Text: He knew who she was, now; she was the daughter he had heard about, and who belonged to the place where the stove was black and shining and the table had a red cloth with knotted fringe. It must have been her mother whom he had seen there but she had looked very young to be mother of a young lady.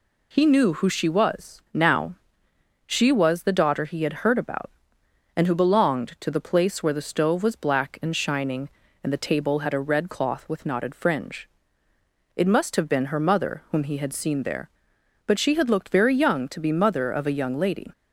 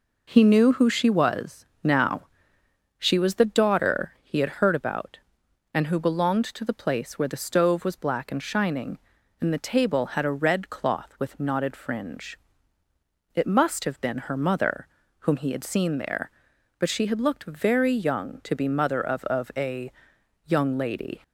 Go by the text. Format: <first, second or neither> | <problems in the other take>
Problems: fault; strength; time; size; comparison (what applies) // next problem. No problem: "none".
first | pauses between "mother" and "whom"; slight; at 14.8 s; 0.34 s long // says "of" twice; at 19.2 s // pauses between "a" and "young"; noticeable; at 19.9 s; 0.54 s long